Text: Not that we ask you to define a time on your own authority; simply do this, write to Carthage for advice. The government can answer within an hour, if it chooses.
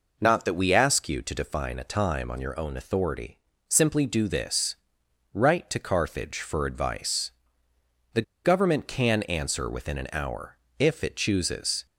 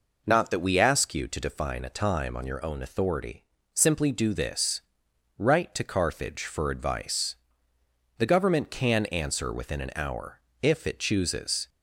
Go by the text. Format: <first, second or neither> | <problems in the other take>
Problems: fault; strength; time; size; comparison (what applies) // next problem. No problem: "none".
second | pauses between "The" and "government"; slight; at 8.2 s; 0.22 s long